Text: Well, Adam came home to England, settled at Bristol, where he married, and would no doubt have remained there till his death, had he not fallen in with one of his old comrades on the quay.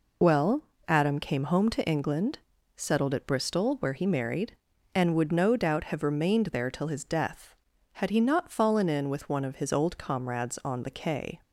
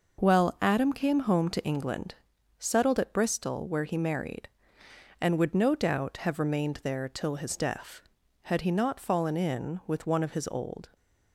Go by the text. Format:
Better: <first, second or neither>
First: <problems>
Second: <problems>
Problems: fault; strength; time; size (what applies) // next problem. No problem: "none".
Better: first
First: none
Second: stops before "comrades on the quay"; at 10.9 s